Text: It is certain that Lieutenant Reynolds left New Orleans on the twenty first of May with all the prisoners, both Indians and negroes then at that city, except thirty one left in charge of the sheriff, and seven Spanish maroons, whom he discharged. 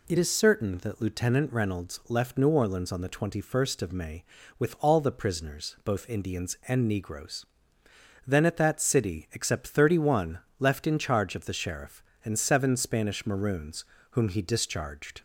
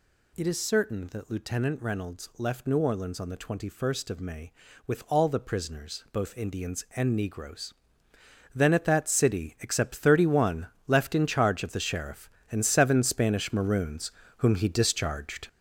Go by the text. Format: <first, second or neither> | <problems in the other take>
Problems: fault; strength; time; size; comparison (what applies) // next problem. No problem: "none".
first | gets louder; throughout; 7 dB // pauses between "negroes" and "then"; noticeable; at 7.7 s; 0.82 s long; noticeable in the first // pauses between "one" and "left"; slight; at 10.6 s; 0.20 s long; slight in the first